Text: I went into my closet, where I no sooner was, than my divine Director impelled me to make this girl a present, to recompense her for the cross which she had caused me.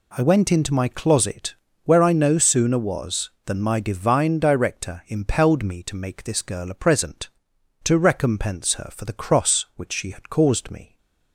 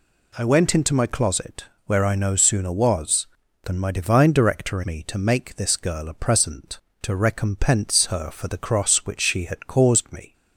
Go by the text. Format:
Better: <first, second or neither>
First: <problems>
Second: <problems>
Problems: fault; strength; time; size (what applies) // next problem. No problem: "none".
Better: first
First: none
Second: skips "impelled"; at 4.8 s